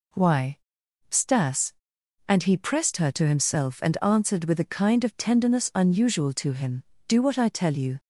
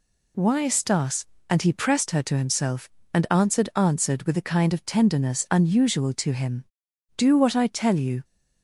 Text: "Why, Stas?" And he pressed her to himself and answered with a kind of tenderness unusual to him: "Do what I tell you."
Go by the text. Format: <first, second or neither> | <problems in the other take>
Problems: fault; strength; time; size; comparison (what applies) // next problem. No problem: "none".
first | says "answered" twice; at 3.7 s